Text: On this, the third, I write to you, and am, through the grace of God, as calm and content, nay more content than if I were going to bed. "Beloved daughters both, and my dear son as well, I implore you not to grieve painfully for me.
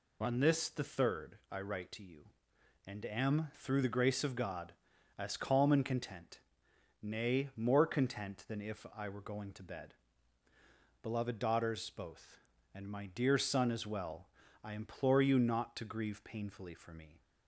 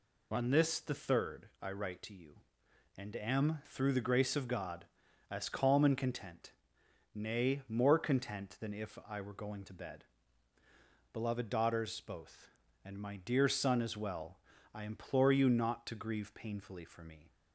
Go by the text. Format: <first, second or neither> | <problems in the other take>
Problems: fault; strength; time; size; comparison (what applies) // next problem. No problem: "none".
neither | none